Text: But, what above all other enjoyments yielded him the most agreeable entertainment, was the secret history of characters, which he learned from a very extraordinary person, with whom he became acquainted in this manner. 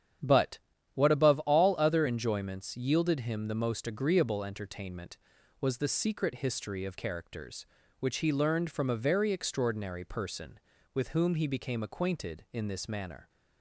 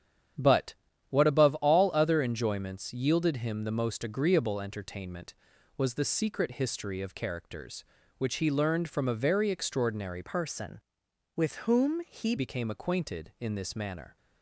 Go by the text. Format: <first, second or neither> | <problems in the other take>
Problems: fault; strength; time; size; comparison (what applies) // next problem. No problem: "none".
first | starts louder than the rest; strong; until 1.7 s; 9 dB; strong in the first // changes voice from "person" to "he"; from 10.2 to 12.3 s; 2.1 s long